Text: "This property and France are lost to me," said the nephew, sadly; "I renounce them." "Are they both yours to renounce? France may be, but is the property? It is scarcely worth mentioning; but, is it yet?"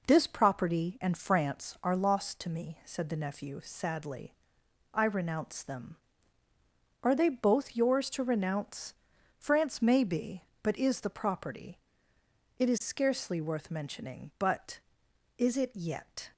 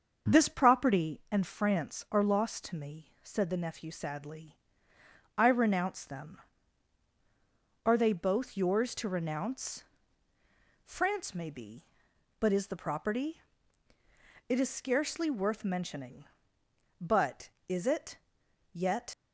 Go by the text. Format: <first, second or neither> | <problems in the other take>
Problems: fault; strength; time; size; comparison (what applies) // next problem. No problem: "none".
first | starts louder than the rest; until 1.3 s; 7 dB // pauses between "it" and "yet"; noticeable; at 18.1 s; 0.54 s long // leaves "yet" unfinished; at 19.1 s; 65 ms